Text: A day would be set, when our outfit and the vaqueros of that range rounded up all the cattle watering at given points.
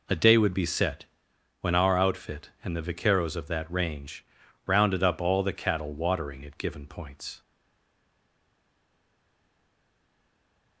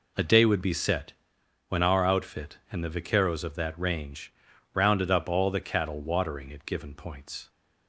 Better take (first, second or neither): second